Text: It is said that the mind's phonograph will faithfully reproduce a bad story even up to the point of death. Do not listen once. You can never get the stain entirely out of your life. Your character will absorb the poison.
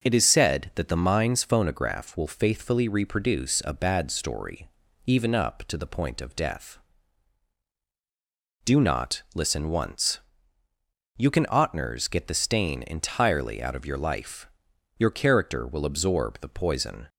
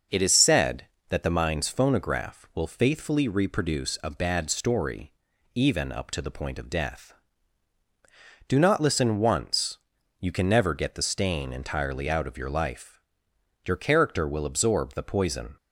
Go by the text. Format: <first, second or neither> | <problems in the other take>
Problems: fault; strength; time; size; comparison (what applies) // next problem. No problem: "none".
second | pauses between "story" and "even"; at 4.6 s; 0.38 s long; also in the second // says "otners" for "never"; at 11.4 s